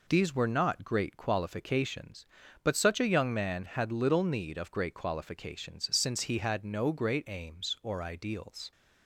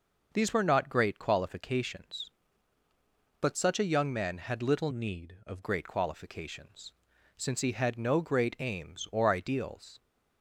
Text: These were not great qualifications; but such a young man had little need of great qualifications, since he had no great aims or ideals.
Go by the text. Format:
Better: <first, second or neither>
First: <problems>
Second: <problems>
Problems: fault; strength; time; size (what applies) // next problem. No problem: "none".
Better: first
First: none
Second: changes voice from "need" to "of"; from 4.9 to 5.6 s; 0.7 s long